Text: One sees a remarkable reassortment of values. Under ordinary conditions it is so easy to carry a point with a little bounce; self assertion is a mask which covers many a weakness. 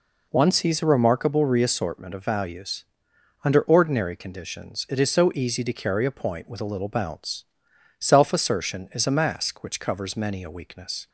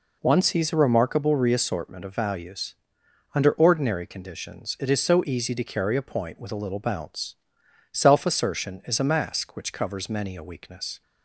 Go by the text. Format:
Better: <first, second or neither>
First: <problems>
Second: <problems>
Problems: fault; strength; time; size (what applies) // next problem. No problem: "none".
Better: neither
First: none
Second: none